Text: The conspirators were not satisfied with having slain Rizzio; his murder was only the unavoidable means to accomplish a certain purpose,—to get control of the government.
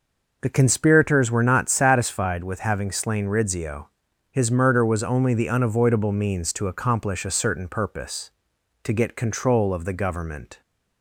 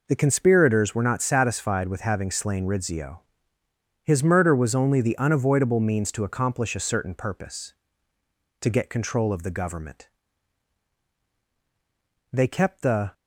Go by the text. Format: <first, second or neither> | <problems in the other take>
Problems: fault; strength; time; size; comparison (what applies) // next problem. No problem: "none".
first | goes on to say "They kept the"; noticeable; from 12.3 s on; 0.80 s long